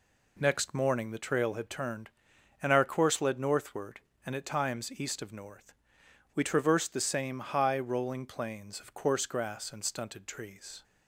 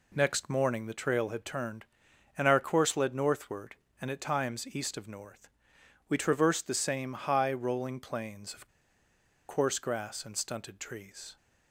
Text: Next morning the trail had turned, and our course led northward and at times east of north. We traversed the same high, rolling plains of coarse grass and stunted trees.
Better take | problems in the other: first | pauses between "of" and "coarse"; noticeable; at 8.6 s; 0.81 s long

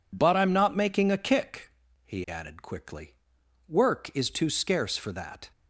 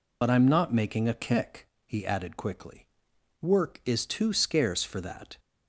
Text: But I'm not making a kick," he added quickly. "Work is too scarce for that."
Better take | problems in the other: first | loses the start of "But"; at 0.2 s; 65 ms

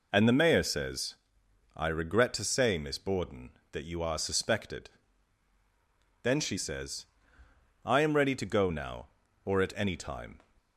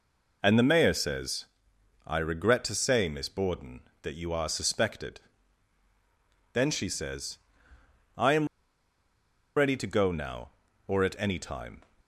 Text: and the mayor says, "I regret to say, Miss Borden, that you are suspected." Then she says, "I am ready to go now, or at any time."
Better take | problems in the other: first | pauses between "am" and "ready"; at 8.4 s; 1.0 s long

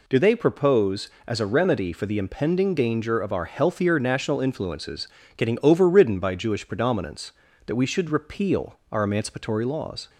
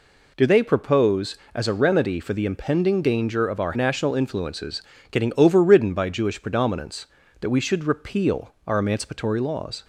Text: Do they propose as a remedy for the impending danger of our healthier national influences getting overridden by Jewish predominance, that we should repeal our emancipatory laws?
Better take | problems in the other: first | skips "healthier"; at 3.7 s // pauses between "influences" and "getting"; slight; at 4.8 s; 0.28 s long; slight in the first

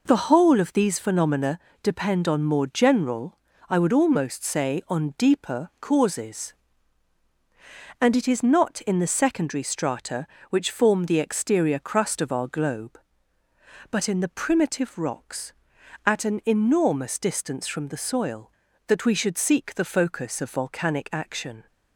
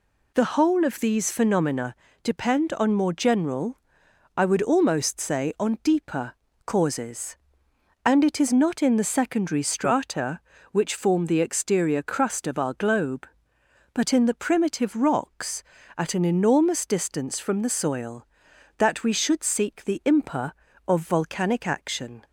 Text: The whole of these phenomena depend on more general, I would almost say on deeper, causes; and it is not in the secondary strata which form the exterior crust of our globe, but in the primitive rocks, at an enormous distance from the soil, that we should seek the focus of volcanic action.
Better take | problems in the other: first | pauses between "phenomena" and "depend"; slight; at 1.9 s; 0.28 s long; slight in the first // says "impa" for "focus"; at 20.0 s

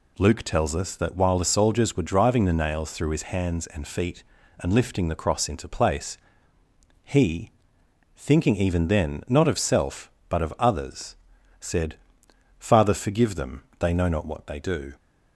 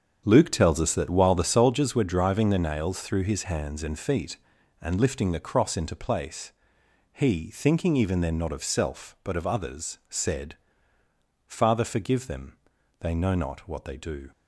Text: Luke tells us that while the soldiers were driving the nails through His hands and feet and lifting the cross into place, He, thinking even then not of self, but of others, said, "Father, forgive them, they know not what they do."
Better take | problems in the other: first | starts louder than the rest; strong; until 1.8 s; 7.5 dB

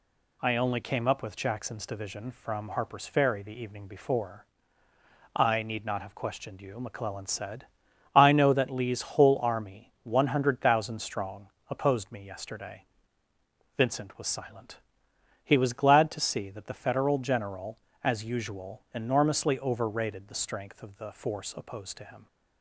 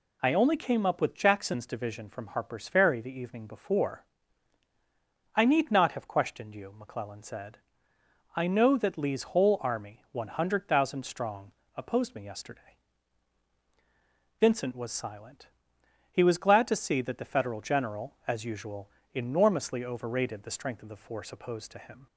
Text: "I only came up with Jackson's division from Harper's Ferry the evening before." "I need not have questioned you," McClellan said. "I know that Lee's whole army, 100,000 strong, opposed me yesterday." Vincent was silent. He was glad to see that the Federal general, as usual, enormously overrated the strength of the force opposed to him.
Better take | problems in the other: neither | none

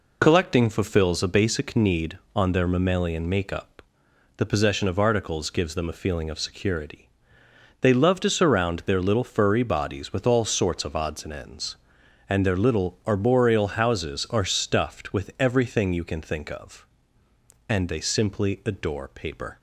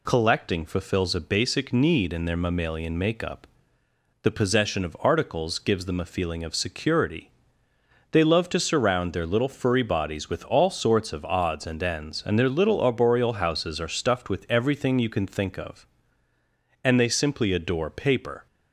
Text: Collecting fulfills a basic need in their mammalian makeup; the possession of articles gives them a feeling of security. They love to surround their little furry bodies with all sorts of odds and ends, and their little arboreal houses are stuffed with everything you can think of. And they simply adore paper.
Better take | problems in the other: second | says "on" for "in"; at 2.3 s

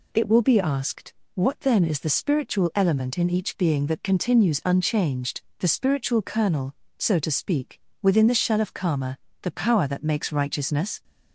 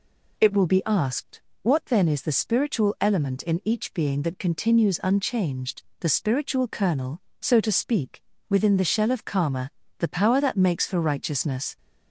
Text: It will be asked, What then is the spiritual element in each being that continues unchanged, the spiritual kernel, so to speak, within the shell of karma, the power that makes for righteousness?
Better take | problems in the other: second | skips "for"; at 10.3 s

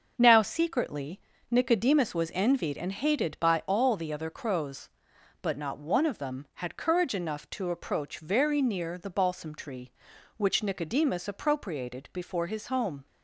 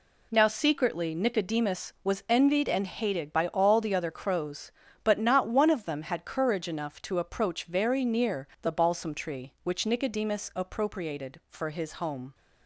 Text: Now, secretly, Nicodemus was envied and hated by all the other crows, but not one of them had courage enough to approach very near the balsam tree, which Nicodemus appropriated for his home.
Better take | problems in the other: second | starts louder than the rest; until 1.1 s; 6.5 dB // says "before" for "for"; at 12.1 s

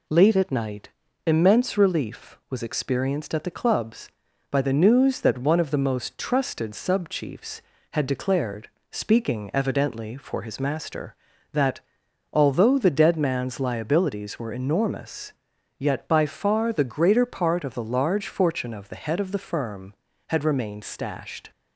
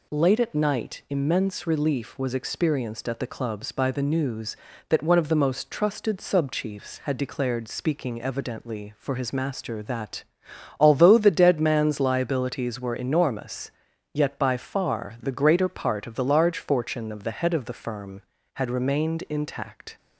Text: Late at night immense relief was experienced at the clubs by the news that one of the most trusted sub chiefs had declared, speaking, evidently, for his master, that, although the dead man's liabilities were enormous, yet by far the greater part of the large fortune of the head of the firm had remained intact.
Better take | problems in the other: second | pauses between "night" and "immense"; slight; at 0.9 s; 0.36 s long // says "stashed" for "intact"; at 20.8 s

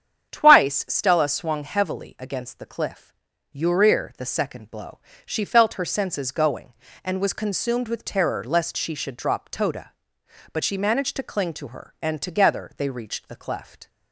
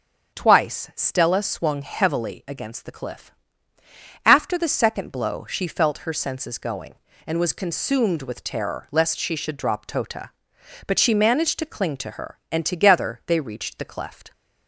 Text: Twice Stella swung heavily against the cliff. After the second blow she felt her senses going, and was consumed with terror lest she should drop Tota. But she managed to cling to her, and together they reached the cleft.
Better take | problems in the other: second | starts louder than the rest; strong; until 1.3 s; 8.5 dB; strong in the second // says "Urir" for "After"; at 3.5 s // pauses between "blow" and "she"; slight; at 4.9 s; 0.26 s long

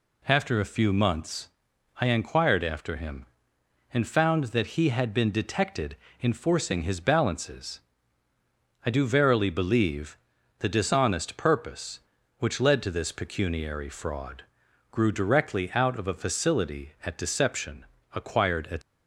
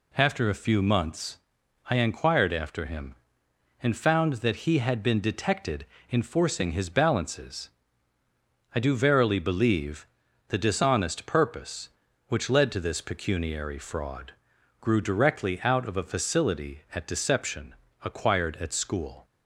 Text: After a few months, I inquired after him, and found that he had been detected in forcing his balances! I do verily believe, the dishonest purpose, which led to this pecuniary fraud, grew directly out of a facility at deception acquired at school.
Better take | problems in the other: second | pauses between "deception" and "acquired"; slight; at 17.8 s; 0.30 s long; slight in the second // stops before "school"; at 18.8 s

